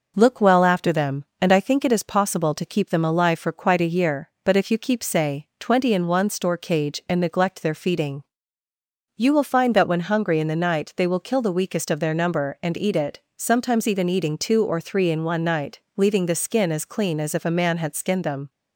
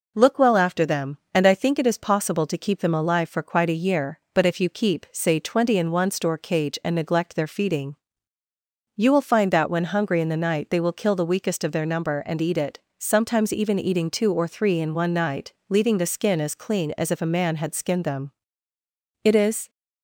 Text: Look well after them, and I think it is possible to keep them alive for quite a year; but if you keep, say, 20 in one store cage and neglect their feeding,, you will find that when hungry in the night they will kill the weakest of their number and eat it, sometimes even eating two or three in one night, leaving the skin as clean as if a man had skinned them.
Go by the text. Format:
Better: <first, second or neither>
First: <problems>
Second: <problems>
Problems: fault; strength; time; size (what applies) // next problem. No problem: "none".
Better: first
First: none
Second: goes on to say "It is"; slight; from 19.2 s on; 0.46 s long